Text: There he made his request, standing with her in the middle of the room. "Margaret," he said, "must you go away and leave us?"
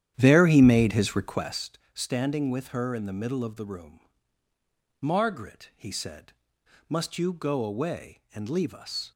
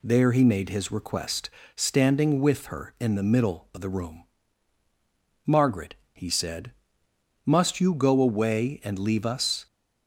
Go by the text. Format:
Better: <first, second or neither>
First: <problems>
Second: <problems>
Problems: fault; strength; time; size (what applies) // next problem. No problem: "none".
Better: second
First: starts louder than the rest; strong; until 1.6 s; 10.5 dB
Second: none